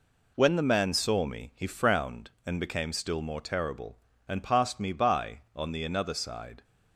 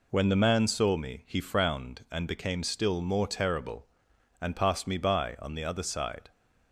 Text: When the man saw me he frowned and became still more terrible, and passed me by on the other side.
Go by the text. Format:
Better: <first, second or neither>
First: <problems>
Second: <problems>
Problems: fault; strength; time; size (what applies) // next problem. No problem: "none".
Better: second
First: says "another" for "other"; at 5.8 s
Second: none